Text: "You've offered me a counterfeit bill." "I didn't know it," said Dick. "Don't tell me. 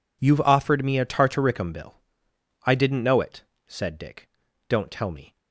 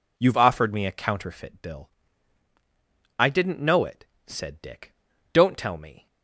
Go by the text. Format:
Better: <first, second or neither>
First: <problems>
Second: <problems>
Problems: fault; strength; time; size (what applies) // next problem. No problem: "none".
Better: second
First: says "tartaricum" for "counterfeit"; at 1.0 s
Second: none